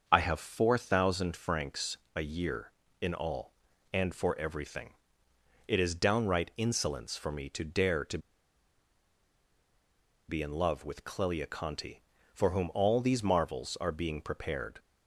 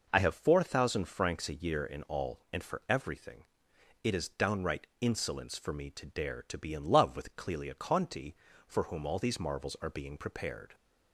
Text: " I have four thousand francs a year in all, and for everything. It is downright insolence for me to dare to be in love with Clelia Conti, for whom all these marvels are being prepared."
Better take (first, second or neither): second